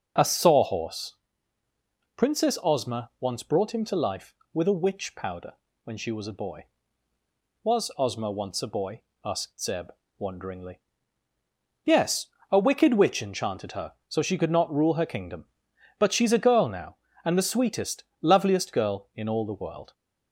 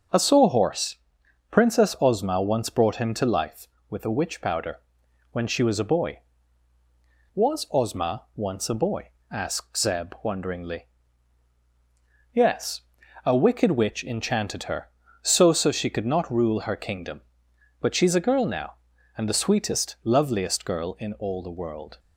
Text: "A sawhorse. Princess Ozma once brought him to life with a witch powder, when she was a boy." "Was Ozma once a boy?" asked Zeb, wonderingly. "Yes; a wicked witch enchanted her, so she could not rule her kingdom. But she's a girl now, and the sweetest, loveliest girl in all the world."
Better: first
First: none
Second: starts louder than the rest; until 1.6 s; 6.5 dB // says "so" twice; at 15.5 s

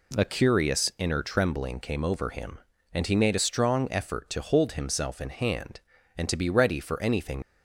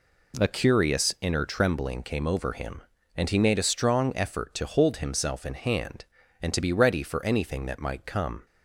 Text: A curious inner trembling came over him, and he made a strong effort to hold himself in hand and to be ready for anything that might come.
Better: second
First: stops before "that might come"; at 7.4 s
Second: none

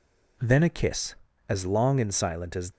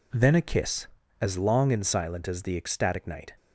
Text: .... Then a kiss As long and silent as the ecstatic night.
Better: second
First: stops before "the ecstatic night"; at 2.7 s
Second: none

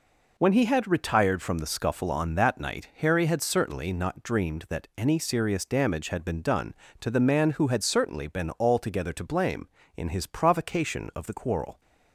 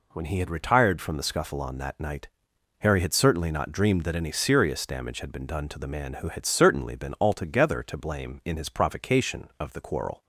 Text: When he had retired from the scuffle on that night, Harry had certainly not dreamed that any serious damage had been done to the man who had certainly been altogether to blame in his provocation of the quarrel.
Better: neither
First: none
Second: none

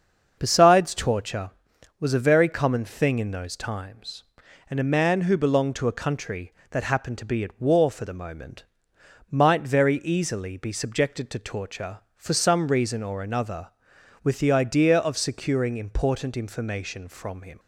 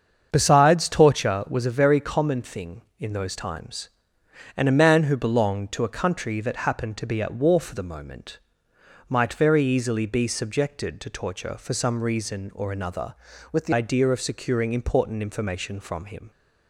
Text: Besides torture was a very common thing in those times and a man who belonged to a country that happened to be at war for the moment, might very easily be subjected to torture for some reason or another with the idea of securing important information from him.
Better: first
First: starts louder than the rest; until 1.4 s; 6.5 dB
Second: starts louder than the rest; until 1.3 s; 7 dB // changes voice from "with" to "the"; from 13.5 to 13.7 s; 0.2 s long

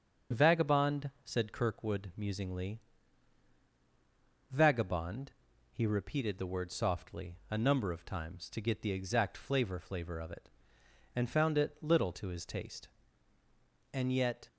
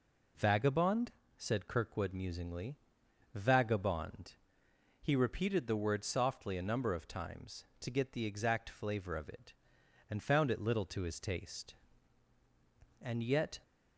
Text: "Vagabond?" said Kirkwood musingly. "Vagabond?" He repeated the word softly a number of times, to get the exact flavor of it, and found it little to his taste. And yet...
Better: second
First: starts louder than the rest; strong; until 1.4 s; 7.5 dB // says "flavor" twice; at 9.7 s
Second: none

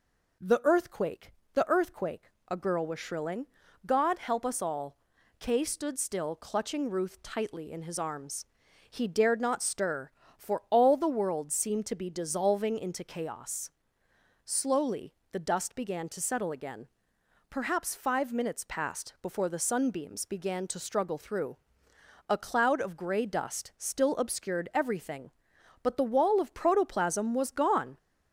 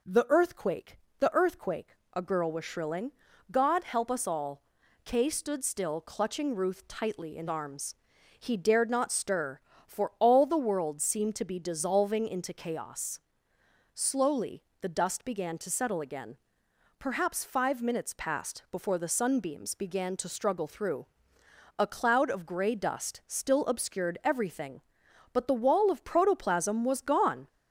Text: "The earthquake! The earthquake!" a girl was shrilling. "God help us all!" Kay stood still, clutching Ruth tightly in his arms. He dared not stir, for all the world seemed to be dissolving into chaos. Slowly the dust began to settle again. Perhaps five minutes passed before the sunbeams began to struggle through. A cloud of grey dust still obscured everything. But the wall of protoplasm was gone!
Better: first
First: pauses between "Slowly" and "the"; slight; at 15.1 s; 0.20 s long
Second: skips "his"; at 7.4 s // pauses between "Slowly" and "the"; slight; at 14.6 s; 0.20 s long

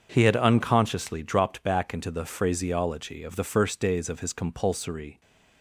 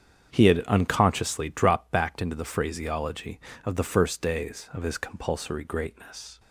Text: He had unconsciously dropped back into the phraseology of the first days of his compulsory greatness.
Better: second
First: starts louder than the rest; strong; until 1.1 s; 7 dB // stops before "greatness"; at 5.2 s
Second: starts louder than the rest; strong; until 1.3 s; 8 dB

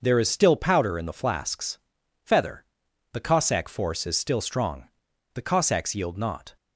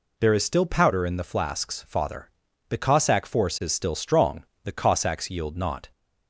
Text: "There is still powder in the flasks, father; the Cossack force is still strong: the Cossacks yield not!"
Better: second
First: starts louder than the rest; noticeable; until 1.0 s; 6 dB // says "feather" for "father"; at 2.2 s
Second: none

